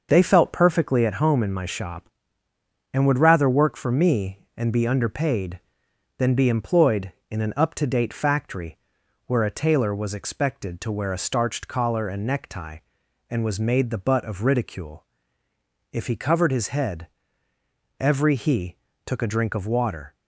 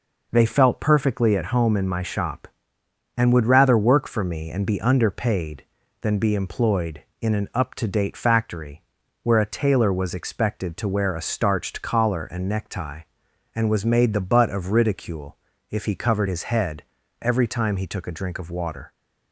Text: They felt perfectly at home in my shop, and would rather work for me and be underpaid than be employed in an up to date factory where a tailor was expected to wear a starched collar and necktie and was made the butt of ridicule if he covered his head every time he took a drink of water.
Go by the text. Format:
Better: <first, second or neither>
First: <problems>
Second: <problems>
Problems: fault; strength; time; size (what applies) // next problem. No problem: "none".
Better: second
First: starts louder than the rest; noticeable; until 1.1 s; 6 dB // pauses between "factory" and "where"; noticeable; at 8.7 s; 0.50 s long // pauses between "ridicule" and "if"; noticeable; at 15.0 s; 0.86 s long // pauses between "head" and "every"; noticeable; at 17.0 s; 0.94 s long // skips "time"; at 18.3 s // pauses between "he" and "took"; slight; at 18.7 s; 0.30 s long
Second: pauses between "factory" and "where"; at 8.8 s; 0.42 s long // pauses between "ridicule" and "if"; slight; at 15.3 s; 0.34 s long // pauses between "head" and "every"; slight; at 16.8 s; 0.36 s long